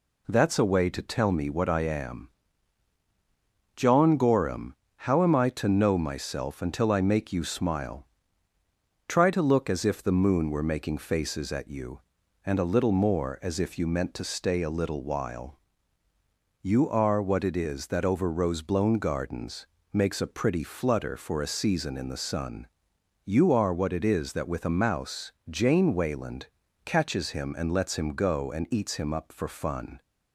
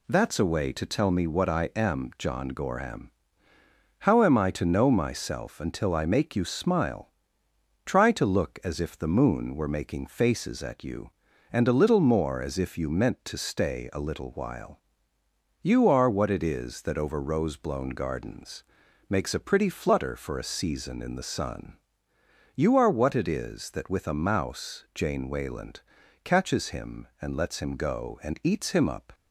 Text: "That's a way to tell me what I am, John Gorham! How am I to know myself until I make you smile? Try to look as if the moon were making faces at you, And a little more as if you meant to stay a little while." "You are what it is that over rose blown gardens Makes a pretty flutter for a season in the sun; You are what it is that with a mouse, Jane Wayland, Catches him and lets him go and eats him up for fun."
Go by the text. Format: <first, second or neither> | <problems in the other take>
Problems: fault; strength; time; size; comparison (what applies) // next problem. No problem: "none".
first | pauses between "gardens" and "Makes"; at 18.6 s; 0.44 s long; slight in the first // stops before "for fun"; at 29.1 s